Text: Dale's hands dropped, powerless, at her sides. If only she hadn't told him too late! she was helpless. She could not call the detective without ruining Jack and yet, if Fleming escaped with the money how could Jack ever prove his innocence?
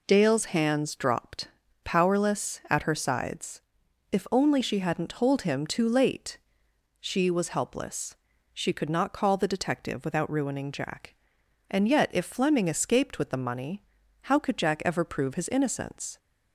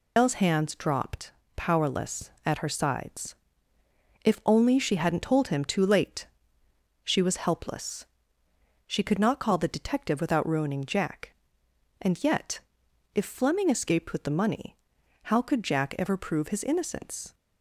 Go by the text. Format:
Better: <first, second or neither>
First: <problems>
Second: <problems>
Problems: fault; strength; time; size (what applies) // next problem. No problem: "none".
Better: first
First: pauses between "money" and "how"; at 13.8 s; 0.42 s long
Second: loses the start of "Dale's"; at 0.1 s; 165 ms // pauses between "money" and "how"; noticeable; at 14.7 s; 0.48 s long